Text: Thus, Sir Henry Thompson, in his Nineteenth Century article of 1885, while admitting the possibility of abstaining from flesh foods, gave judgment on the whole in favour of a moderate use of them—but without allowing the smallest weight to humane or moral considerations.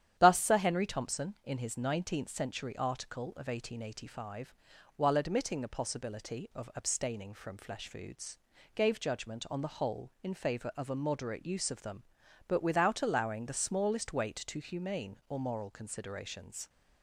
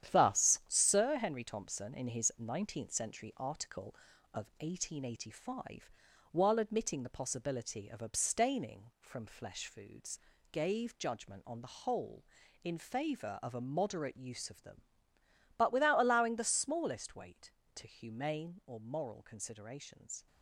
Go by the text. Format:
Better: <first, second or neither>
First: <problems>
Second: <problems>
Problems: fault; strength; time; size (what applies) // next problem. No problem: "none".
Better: first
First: starts louder than the rest; strong; until 1.1 s; 10 dB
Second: gets quieter; throughout; 6.5 dB // starts louder than the rest; strong; until 1.1 s; 9.5 dB